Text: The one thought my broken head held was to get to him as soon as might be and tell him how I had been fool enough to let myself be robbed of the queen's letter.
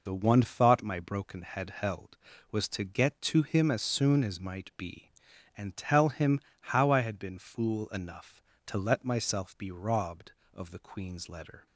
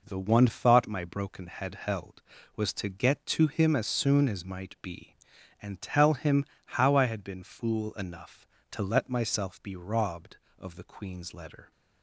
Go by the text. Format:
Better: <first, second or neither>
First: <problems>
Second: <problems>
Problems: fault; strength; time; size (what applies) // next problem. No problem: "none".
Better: second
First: loses the start of "The"; at 0.0 s; 50 ms // pauses between "him" and "how"; slight; at 6.3 s; 0.32 s long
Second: pauses between "him" and "how"; slight; at 6.4 s; 0.32 s long